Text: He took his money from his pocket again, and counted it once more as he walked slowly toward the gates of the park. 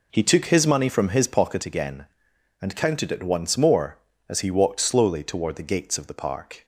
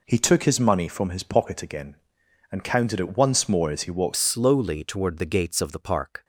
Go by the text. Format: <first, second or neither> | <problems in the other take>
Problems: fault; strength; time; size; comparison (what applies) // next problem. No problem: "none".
first | changes voice at "slowly"; from 4.1 s on; 2.1 s long